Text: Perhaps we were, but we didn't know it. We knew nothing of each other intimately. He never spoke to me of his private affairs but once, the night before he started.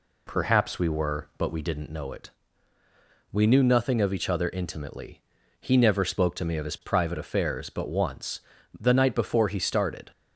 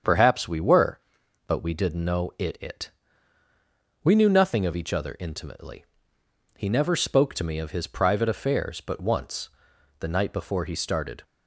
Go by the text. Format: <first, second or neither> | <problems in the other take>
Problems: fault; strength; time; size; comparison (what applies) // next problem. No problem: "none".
first | starts louder than the rest; strong; until 1.5 s; 7.5 dB // says "it" twice; at 2.6 s